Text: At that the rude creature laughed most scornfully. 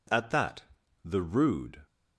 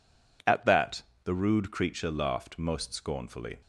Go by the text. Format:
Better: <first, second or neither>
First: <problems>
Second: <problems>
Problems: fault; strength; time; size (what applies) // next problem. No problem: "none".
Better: second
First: pauses between "that" and "the"; at 0.6 s; 0.42 s long // stops before "creature laughed most scornfully"; at 1.8 s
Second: pauses between "that" and "the"; slight; at 1.0 s; 0.22 s long